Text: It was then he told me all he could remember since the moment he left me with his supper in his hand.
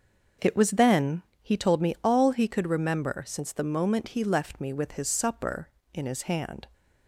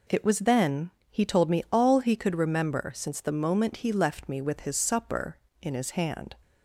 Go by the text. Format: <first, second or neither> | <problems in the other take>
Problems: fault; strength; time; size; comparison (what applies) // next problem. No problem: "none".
second | starts louder than the rest; noticeable; until 1.5 s; 6 dB // pauses between "then" and "he"; slight; at 1.2 s; 0.20 s long; slight in the second